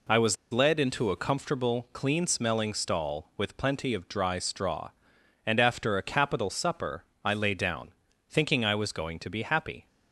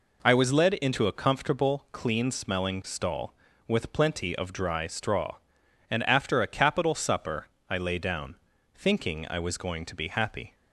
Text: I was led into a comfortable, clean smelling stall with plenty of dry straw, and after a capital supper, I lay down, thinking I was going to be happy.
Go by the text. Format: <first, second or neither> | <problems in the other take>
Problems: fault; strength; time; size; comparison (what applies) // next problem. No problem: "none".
second | pauses between "was" and "led"; slight; at 0.3 s; 0.16 s long